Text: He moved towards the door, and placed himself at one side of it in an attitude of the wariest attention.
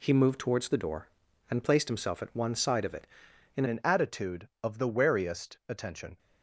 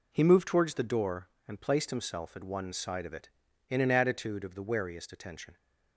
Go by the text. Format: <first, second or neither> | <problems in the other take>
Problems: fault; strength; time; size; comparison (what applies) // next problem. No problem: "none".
second | changes voice at "an"; from 3.6 s on; 2.5 s long